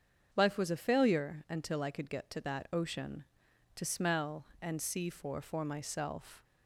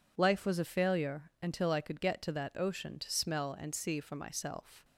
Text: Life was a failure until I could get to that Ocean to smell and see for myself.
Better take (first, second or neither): second